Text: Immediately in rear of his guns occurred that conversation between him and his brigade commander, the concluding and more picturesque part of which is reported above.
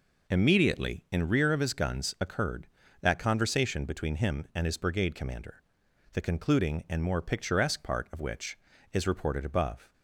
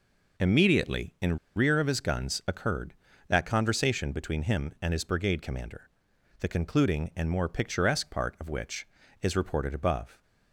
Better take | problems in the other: first | pauses between "in" and "rear"; slight; at 1.3 s; 0.17 s long

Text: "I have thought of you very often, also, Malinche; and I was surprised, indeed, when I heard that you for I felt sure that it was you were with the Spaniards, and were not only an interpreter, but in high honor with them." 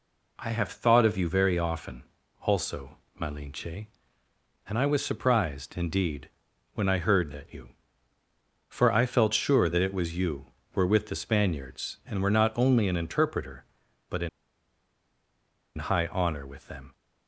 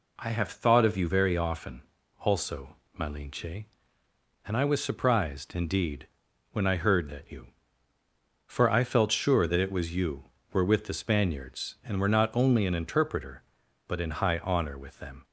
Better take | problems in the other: second | pauses between "in" and "high"; strong; at 14.2 s; 1.4 s long

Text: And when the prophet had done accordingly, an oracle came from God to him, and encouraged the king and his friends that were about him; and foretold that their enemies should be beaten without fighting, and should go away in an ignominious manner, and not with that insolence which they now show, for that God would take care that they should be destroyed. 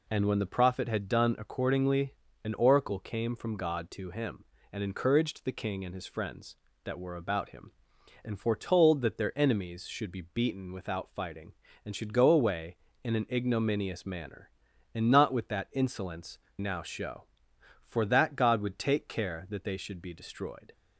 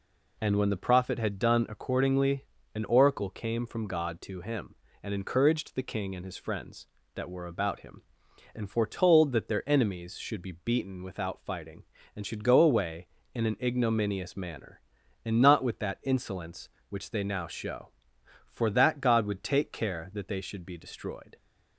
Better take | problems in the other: second | skips "which they"; at 16.4 s

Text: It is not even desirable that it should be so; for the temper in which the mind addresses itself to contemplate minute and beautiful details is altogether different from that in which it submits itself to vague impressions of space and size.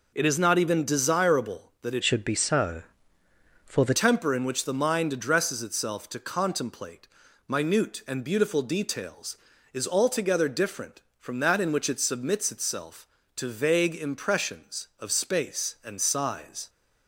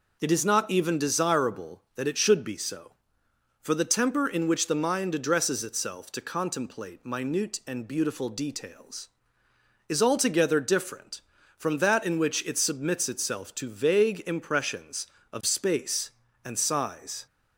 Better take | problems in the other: second | changes voice from "should" to "the"; from 2.0 to 3.9 s; 1.9 s long // pauses between "contemplate" and "minute"; at 7.0 s; 0.40 s long

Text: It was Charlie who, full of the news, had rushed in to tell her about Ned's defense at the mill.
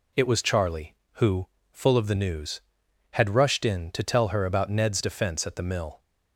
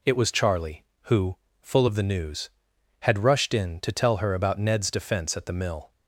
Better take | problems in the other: neither | none

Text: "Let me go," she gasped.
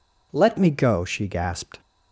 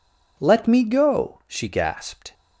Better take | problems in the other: second | changes voice at "me"; from 0.5 s on; 1.3 s long

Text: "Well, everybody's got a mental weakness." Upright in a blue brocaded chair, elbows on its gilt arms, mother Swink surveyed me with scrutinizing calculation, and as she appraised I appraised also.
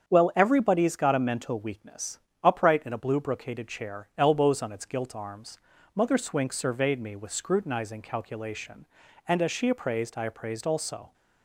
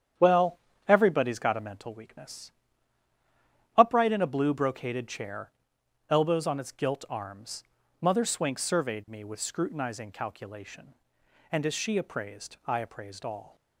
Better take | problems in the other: first | starts louder than the rest; strong; until 1.4 s; 9 dB; strong in the first // says "all" for "also"; at 13.2 s

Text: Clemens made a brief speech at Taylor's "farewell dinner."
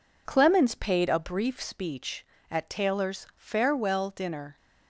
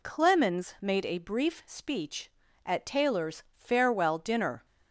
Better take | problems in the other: second | says "paid" for "made"; at 0.7 s

